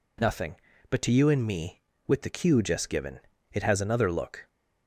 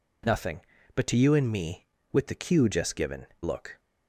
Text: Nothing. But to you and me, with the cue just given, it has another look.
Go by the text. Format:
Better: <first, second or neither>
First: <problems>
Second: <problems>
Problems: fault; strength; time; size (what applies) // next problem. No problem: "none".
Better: first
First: none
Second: skips "it has another"; at 3.3 s